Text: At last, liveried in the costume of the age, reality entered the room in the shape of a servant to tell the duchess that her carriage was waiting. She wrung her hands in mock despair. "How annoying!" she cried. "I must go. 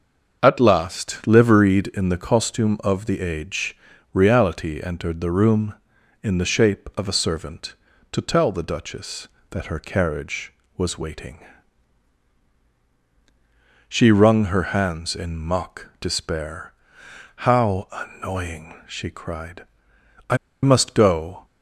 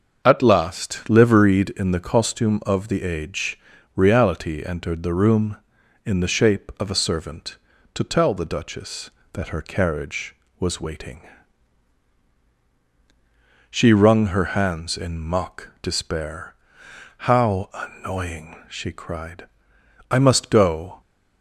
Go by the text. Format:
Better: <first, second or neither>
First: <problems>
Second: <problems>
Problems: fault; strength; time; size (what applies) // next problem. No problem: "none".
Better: second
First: starts louder than the rest; until 1.4 s; 6.5 dB // pauses between "I" and "must"; slight; at 20.3 s; 0.25 s long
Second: starts louder than the rest; until 1.2 s; 6.5 dB